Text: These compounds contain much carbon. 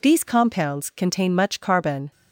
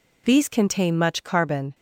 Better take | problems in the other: first | skips "compounds"; at 0.4 s

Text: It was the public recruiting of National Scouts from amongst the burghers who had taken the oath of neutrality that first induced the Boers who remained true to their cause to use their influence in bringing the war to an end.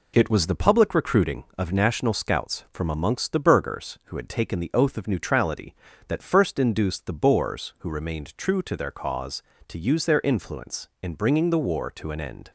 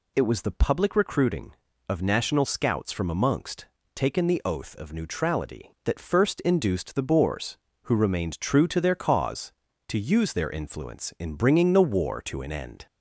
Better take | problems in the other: first | skips "the burghers who had"; at 3.8 s

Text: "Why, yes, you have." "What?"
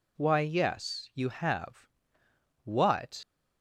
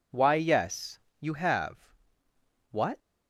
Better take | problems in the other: second | leaves "What" unfinished; at 3.2 s; 85 ms

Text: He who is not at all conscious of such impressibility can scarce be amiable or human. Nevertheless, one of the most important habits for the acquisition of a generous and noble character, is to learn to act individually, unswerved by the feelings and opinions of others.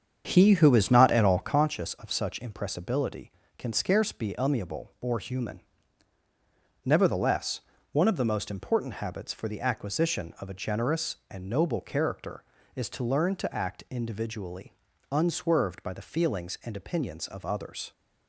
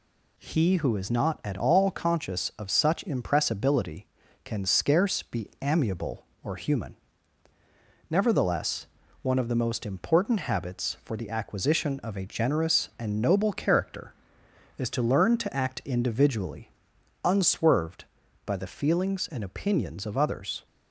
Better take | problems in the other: second | starts louder than the rest; strong; until 1.7 s; 7.5 dB

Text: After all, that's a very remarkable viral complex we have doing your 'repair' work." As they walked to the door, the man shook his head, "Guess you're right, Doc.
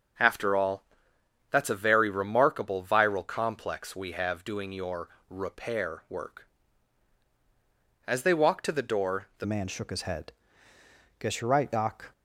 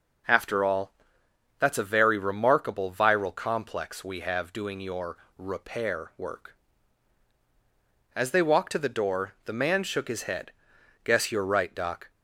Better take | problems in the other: second | pauses between "your" and "repair"; slight; at 5.0 s; 0.20 s long; slight in the second // changes voice at "man"; from 9.4 s on; 2.7 s long

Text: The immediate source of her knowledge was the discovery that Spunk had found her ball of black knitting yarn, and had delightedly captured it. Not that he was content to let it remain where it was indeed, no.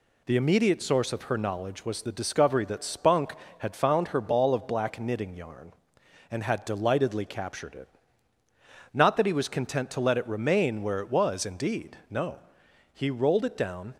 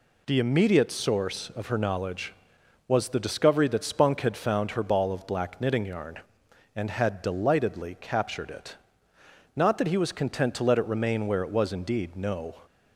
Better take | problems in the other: second | goes on to say "He rolled it down"; noticeable; from 12.9 s on; 1.0 s long

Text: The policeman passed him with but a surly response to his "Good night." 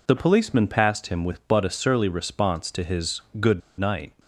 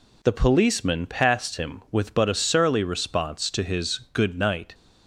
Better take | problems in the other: second | pauses between "his" and "Good"; slight; at 3.2 s; 0.18 s long; slight in the second // pauses between "Good" and "night"; slight; at 3.6 s; 0.20 s long

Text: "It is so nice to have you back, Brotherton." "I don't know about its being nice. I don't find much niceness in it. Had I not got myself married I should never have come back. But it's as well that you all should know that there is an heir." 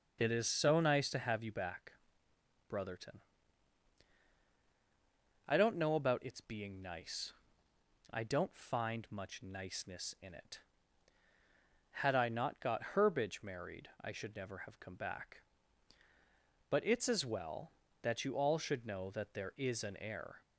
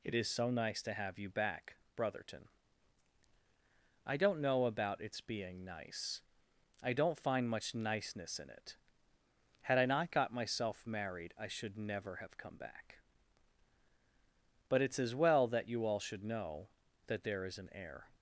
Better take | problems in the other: second | says "herbage" for "myself"; at 12.9 s

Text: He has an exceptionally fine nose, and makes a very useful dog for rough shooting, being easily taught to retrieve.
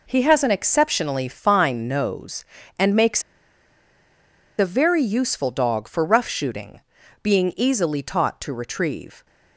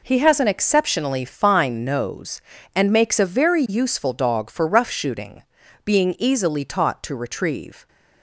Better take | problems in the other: second | pauses between "makes" and "a"; strong; at 3.2 s; 1.3 s long

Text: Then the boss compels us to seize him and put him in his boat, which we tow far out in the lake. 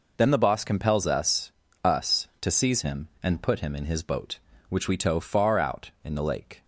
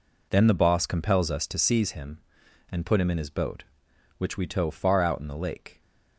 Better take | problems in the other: second | says "us" twice; at 1.8 s

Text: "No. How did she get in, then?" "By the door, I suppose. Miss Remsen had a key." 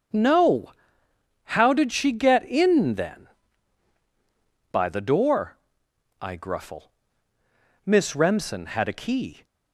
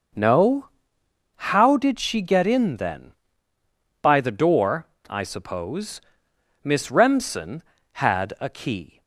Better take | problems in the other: second | starts louder than the rest; strong; until 1.9 s; 7 dB; noticeable in the second // says "gruffle" for "suppose"; at 6.3 s

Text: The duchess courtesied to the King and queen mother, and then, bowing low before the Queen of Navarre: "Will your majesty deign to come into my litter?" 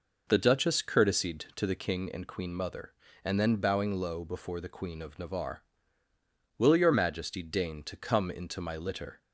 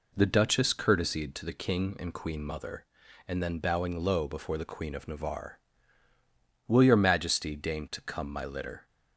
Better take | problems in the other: first | skips "into"; at 8.3 s

